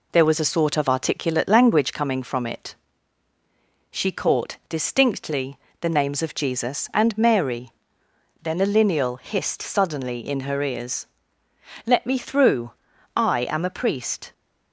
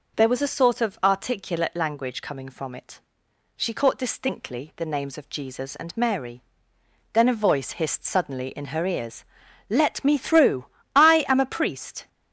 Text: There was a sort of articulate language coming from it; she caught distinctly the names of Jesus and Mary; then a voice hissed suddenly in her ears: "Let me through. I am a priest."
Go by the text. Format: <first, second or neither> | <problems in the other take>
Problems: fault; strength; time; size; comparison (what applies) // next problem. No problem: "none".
second | pauses between "distinctly" and "the"; slight; at 5.5 s; 0.26 s long // says "lineal" for "voice"; at 8.6 s